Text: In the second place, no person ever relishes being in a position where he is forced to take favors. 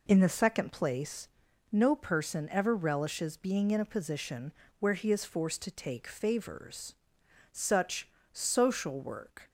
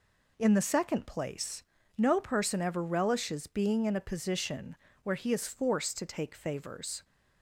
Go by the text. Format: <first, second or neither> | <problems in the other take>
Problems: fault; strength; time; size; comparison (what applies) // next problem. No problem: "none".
second | pauses between "position" and "where"; slight; at 4.5 s; 0.26 s long; slight in the second // goes on to say "Such social work"; strong; from 7.5 s on; 1.9 s long